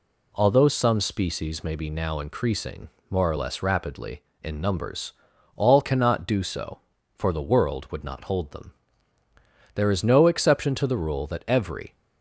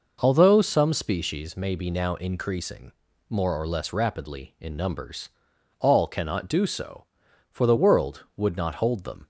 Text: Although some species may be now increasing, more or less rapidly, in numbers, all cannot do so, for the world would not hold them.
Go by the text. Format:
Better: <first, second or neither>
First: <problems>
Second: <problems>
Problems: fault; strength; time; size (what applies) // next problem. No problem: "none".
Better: second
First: goes on to say "There is no exception to the rule that every"; strong; from 9.7 s on; 2.2 s long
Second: none